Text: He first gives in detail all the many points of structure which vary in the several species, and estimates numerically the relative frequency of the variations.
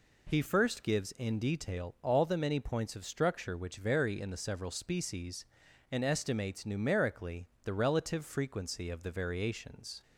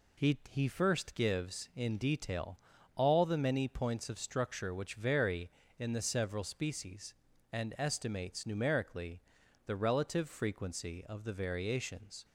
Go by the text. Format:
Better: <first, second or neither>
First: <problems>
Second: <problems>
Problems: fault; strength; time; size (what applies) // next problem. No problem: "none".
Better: first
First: pauses between "numerically" and "the"; slight; at 7.4 s; 0.16 s long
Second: says "He" twice; at 0.4 s // pauses between "detail" and "all"; at 2.5 s; 0.38 s long // pauses between "numerically" and "the"; noticeable; at 9.2 s; 0.46 s long